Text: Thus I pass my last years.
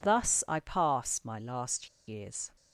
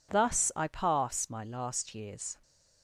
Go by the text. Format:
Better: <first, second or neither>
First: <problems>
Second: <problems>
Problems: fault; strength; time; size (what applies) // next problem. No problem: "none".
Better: second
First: pauses between "last" and "years"; slight; at 1.8 s; 0.19 s long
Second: none